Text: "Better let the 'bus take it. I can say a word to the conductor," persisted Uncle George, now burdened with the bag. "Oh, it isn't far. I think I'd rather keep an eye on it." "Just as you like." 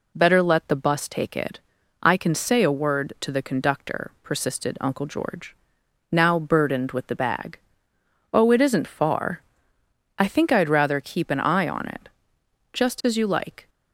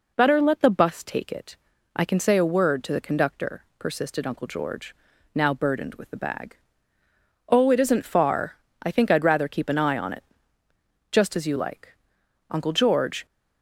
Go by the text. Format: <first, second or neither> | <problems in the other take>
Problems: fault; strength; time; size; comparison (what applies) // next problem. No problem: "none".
first | goes on to say "Uncle George"; noticeable; from 12.4 s on; 0.76 s long